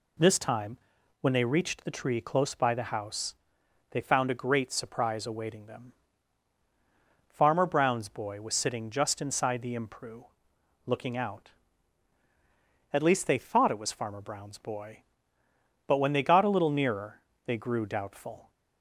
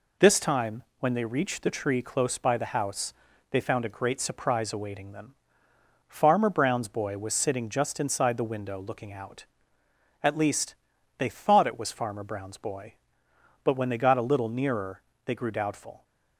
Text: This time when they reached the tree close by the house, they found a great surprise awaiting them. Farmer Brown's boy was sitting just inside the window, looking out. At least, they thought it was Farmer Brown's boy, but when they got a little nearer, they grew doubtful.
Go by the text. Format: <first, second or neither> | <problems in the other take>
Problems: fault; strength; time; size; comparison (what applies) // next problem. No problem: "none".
second | pauses between "time" and "when"; at 0.7 s; 0.42 s long; slight in the second // says "impru" for "window"; at 9.7 s